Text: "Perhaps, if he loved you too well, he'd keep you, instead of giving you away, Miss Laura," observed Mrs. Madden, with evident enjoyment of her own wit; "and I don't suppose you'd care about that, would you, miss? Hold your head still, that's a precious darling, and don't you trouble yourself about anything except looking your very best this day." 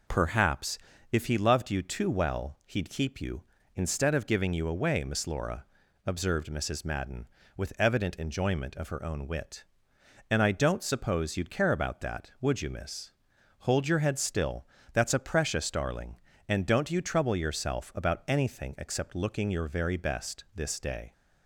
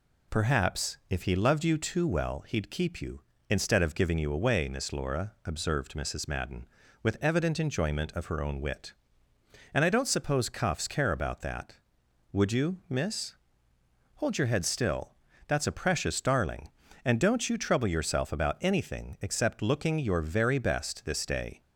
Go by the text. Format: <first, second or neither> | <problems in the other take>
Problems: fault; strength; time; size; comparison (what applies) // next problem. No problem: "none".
first | says "cuffs" for "you'd"; at 10.4 s